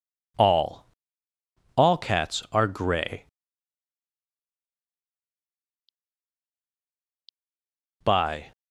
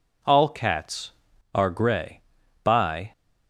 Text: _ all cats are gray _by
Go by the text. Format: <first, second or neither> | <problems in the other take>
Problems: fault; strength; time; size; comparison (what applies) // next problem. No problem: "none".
second | says "all" twice; at 1.7 s